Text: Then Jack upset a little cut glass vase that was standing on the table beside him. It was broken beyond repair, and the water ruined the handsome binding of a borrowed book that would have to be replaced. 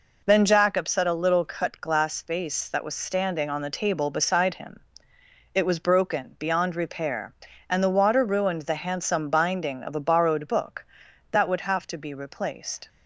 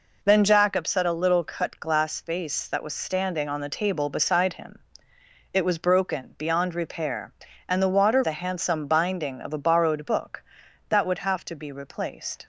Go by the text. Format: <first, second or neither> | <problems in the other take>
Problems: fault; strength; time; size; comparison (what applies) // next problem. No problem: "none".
first | skips "ruined"; at 8.2 s